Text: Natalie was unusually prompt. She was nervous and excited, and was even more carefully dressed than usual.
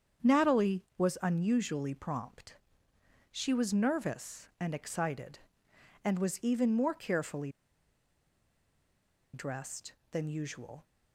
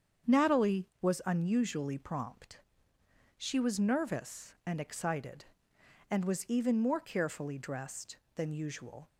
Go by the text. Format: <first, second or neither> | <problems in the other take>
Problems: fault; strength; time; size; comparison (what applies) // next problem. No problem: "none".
second | starts louder than the rest; strong; until 1.4 s; 7.5 dB; strong in the second // pauses between "carefully" and "dressed"; strong; at 7.5 s; 1.8 s long